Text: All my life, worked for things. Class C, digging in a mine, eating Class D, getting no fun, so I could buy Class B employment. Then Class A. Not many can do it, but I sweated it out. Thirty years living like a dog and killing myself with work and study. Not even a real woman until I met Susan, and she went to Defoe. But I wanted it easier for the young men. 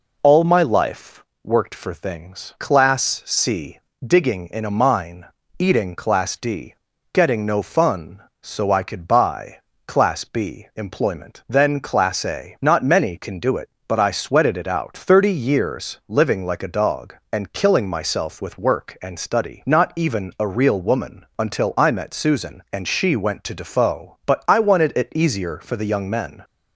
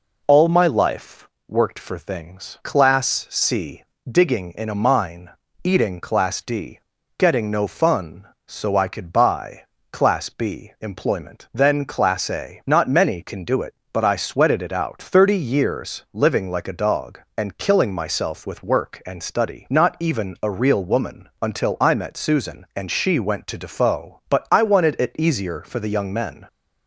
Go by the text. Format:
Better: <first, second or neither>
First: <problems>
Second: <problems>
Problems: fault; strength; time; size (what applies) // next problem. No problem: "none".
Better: neither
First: pauses between "buy" and "Class"; slight; at 9.5 s; 0.26 s long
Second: pauses between "buy" and "Class"; slight; at 9.6 s; 0.26 s long